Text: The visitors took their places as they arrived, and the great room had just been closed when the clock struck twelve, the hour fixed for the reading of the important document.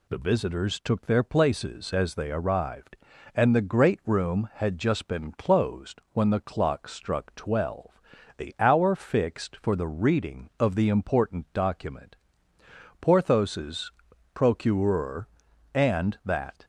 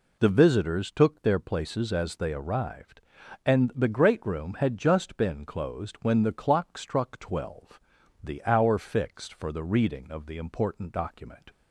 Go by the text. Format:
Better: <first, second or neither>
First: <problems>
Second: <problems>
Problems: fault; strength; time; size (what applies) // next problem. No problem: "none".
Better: second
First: goes on to say "Porthos's procureur and that"; strong; from 13.0 s on; 3.6 s long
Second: none